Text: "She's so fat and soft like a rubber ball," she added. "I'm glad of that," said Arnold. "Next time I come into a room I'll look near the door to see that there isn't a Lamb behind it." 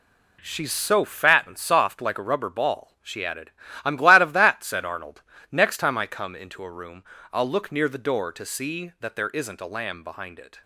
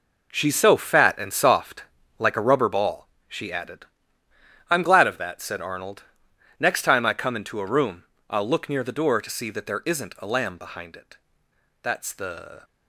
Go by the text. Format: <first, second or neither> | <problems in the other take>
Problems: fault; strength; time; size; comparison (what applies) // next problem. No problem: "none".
first | pauses between "soft" and "like"; slight; at 1.8 s; 0.34 s long // pauses between "room" and "I'll"; slight; at 8.0 s; 0.26 s long; slight in the first // goes on to say "That's the"; noticeable; from 11.8 s on; 0.82 s long